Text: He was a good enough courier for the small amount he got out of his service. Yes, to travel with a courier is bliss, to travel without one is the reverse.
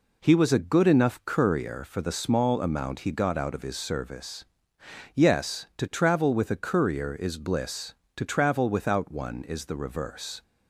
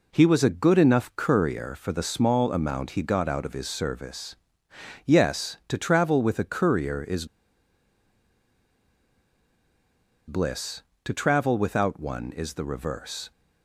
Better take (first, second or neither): first